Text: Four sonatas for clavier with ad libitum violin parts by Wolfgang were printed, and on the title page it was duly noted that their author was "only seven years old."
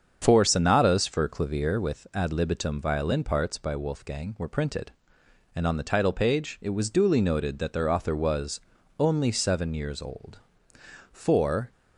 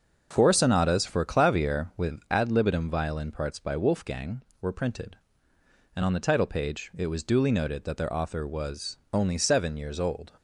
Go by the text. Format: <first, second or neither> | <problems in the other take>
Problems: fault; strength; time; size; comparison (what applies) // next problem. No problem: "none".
second | starts louder than the rest; strong; until 1.2 s; 7 dB; noticeable in the second // pauses between "was" and "only"; at 8.5 s; 0.40 s long; slight in the second // goes on to say "For"; from 11.1 s on; 0.60 s long